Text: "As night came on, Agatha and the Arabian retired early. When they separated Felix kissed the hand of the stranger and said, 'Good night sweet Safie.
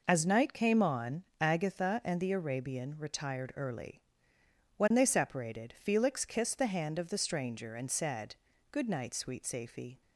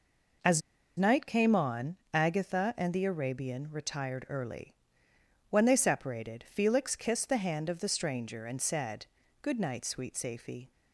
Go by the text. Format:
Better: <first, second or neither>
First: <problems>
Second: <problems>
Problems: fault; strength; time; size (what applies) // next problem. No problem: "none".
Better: first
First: none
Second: pauses between "As" and "night"; at 0.6 s; 0.38 s long